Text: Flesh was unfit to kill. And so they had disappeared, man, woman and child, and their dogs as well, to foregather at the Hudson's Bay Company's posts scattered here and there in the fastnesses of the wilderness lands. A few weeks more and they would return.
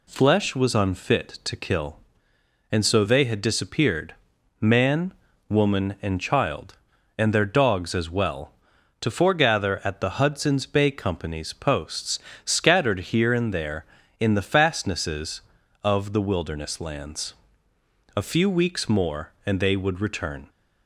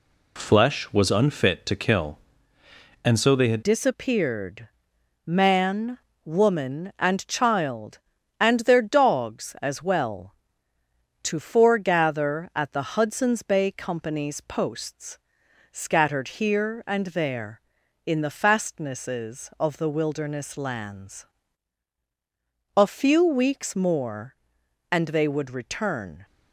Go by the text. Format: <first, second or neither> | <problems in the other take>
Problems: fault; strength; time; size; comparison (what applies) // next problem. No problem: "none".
first | changes voice at "disappeared"; from 3.6 s on; 22.6 s long // pauses between "posts" and "scattered"; noticeable; at 15.1 s; 0.52 s long; slight in the first